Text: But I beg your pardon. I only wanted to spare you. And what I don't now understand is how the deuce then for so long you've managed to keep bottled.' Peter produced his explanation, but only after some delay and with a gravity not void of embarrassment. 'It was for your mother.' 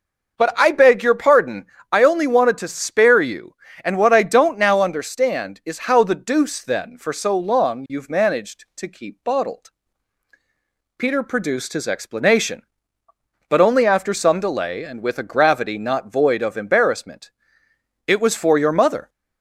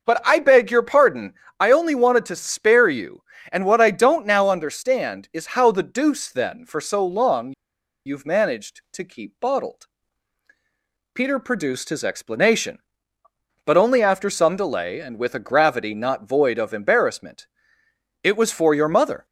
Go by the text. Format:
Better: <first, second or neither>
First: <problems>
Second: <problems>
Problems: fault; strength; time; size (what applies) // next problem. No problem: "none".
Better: first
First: none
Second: pauses between "long" and "you've"; noticeable; at 7.5 s; 0.52 s long